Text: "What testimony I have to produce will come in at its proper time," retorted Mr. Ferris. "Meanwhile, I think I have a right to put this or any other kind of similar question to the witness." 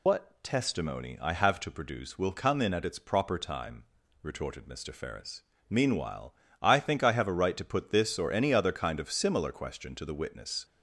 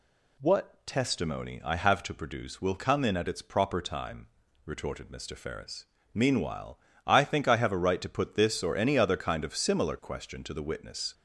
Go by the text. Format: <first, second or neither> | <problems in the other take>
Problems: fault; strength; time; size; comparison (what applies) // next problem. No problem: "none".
second | loses the start of "What"; at 0.0 s; 95 ms